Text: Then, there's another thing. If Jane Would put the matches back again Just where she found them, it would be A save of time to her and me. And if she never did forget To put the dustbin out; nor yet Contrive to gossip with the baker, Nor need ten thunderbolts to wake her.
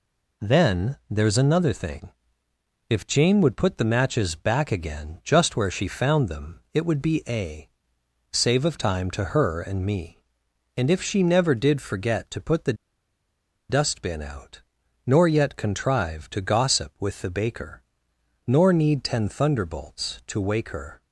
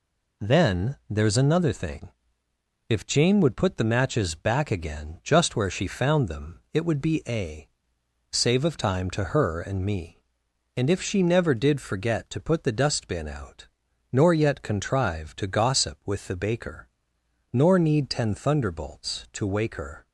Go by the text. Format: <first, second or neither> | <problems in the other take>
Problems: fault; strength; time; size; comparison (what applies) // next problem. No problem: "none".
second | pauses between "A" and "save"; noticeable; at 7.6 s; 0.64 s long; noticeable in the second // pauses between "the" and "dustbin"; noticeable; at 12.7 s; 0.95 s long